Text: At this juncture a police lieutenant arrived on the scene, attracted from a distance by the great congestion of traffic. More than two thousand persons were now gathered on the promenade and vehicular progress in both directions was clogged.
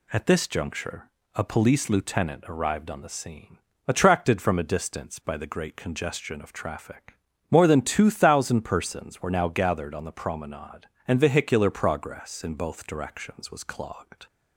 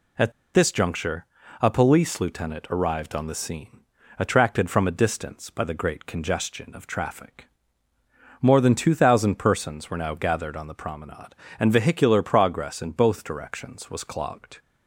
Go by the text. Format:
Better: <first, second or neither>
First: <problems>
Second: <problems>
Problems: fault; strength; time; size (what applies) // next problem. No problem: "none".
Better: first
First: pauses between "juncture" and "a"; slight; at 1.0 s; 0.24 s long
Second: pauses between "At" and "this"; slight; at 0.3 s; 0.21 s long // pauses between "juncture" and "a"; slight; at 1.2 s; 0.36 s long